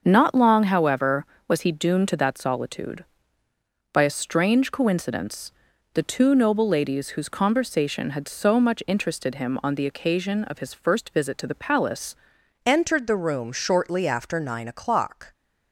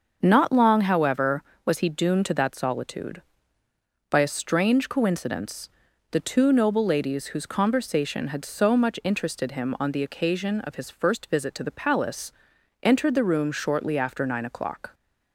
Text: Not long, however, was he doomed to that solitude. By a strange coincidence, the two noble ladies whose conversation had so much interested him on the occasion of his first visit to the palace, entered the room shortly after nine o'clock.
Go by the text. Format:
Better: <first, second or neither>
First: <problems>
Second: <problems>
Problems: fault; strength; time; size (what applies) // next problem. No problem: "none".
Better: second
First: starts louder than the rest; until 1.0 s; 6.5 dB // changes voice at "entered"; from 12.6 s on; 2.7 s long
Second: starts louder than the rest; until 1.2 s; 6.5 dB